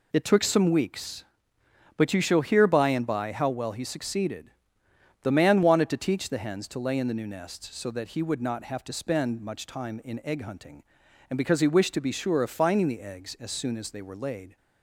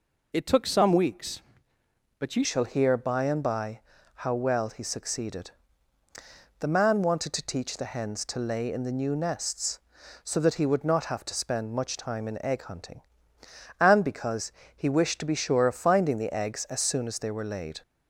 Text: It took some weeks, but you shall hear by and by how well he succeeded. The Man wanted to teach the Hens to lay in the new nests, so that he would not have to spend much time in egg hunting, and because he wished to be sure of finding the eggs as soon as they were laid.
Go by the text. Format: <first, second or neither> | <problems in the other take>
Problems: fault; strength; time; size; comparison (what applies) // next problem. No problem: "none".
first | changes voice at "shall"; from 2.4 s on; 15.4 s long // pauses between "by" and "how"; at 3.8 s; 0.44 s long // pauses between "because" and "he"; slight; at 14.5 s; 0.24 s long